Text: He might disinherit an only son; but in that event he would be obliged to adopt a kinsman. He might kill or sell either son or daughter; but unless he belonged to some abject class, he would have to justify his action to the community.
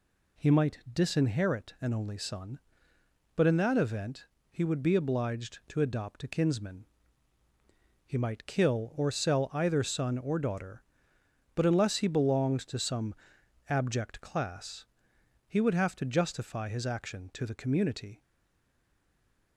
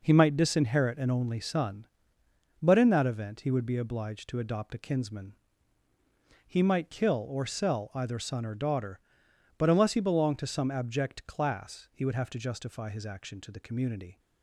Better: second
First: pauses between "event" and "he"; slight; at 4.2 s; 0.24 s long // pauses between "some" and "abject"; noticeable; at 13.1 s; 0.52 s long // stays silent after the last word; noticeable; from 18.2 s on; 1.3 s long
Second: none

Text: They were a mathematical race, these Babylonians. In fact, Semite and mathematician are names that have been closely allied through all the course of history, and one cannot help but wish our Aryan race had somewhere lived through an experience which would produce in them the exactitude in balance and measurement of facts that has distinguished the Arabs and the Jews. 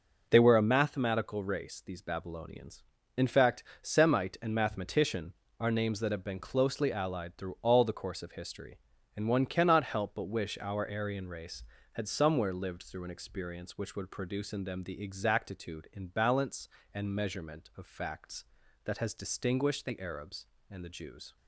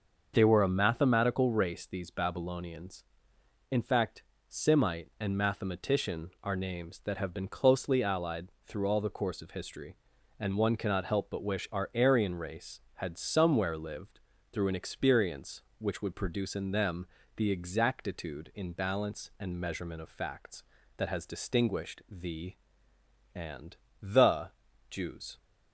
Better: first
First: none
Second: starts louder than the rest; until 1.3 s; 6.5 dB // pauses between "allied" and "through"; slight; at 8.4 s; 0.18 s long // pauses between "lived" and "through"; slight; at 14.1 s; 0.32 s long // pauses between "them" and "the"; slight; at 17.0 s; 0.30 s long // skips "Arabs"; at 22.9 s // pauses between "and" and "the"; slight; at 23.7 s; 0.26 s long // pauses between "the" and "Jews"; at 24.4 s; 0.40 s long

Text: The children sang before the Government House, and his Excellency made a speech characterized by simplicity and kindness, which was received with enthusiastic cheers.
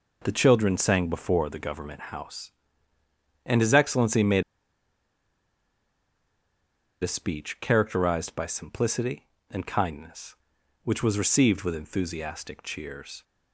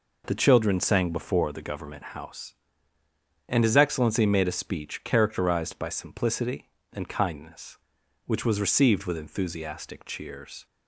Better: second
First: pauses between "made" and "a"; strong; at 4.4 s; 2.6 s long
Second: none

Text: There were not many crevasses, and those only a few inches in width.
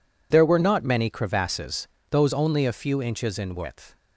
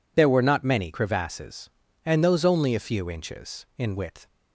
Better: second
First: skips "and"; at 1.9 s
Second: none

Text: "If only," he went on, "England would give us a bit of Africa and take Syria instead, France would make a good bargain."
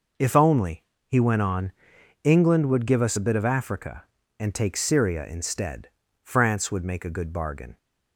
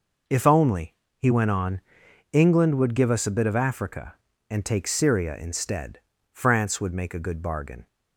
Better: neither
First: none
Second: none

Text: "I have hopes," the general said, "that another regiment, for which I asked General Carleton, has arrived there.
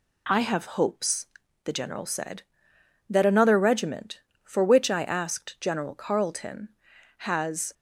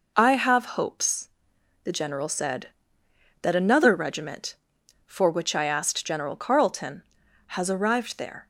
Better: second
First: stops before "arrived there"; at 7.7 s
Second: none

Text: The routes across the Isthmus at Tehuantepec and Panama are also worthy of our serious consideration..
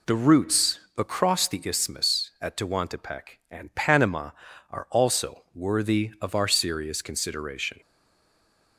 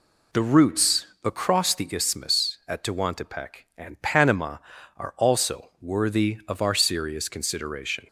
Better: second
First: pauses between "routes" and "across"; slight; at 0.8 s; 0.18 s long // stays silent after the last word; from 7.8 s on; 0.9 s long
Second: pauses between "routes" and "across"; slight; at 1.0 s; 0.18 s long

